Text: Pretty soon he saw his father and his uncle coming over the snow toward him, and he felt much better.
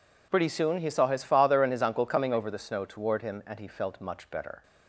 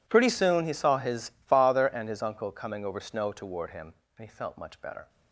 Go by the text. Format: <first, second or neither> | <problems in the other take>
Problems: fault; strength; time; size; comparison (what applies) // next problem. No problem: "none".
first | skips "the"; at 3.0 s